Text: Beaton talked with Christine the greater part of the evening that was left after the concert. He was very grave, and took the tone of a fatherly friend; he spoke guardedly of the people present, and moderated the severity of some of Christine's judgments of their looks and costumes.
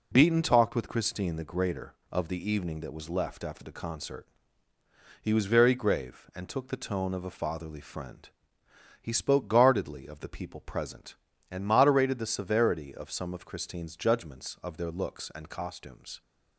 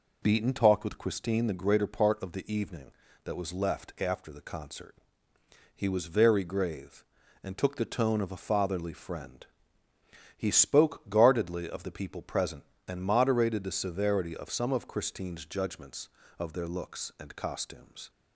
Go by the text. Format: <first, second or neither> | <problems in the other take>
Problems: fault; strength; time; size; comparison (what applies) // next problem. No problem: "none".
second | skips "part"; at 2.0 s